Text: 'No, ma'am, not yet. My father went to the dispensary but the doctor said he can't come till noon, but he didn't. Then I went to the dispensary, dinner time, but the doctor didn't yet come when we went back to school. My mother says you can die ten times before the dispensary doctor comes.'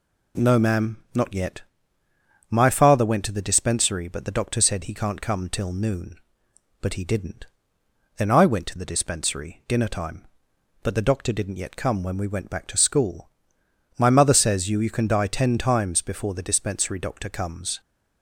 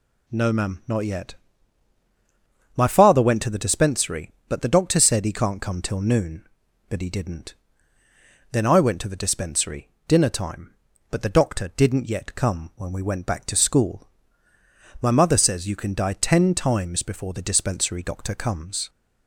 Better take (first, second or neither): second